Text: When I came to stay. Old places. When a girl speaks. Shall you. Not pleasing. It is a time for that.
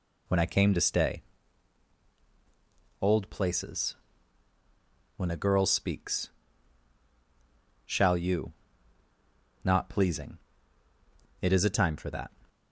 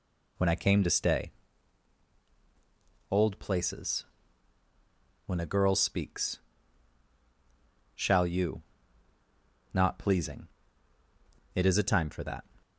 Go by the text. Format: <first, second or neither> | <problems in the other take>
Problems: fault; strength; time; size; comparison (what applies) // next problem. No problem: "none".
neither | none